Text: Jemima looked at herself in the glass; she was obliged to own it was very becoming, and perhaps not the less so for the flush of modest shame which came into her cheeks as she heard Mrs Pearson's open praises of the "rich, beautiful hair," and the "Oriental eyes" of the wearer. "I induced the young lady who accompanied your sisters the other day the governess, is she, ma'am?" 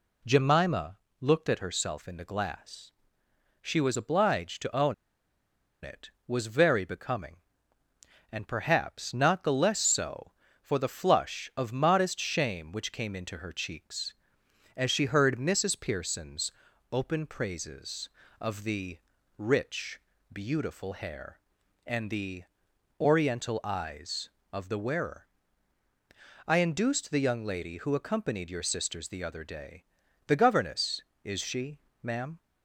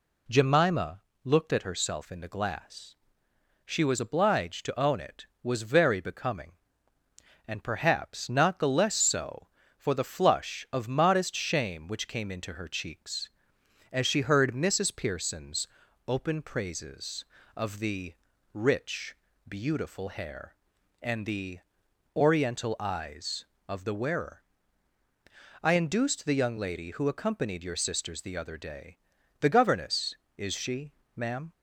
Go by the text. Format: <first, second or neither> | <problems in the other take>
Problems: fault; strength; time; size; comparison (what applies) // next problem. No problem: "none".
second | pauses between "Jemima" and "looked"; slight; at 0.9 s; 0.24 s long; slight in the second // pauses between "own" and "it"; noticeable; at 4.9 s; 0.89 s long // pauses between "Pearson's" and "open"; at 16.5 s; 0.40 s long; also in the second // pauses between "the" and "rich"; at 18.9 s; 0.38 s long; also in the second // pauses between "the" and "Oriental"; noticeable; at 22.4 s; 0.56 s long; noticeable in the second // pauses between "day" and "the"; at 29.8 s; 0.44 s long; also in the second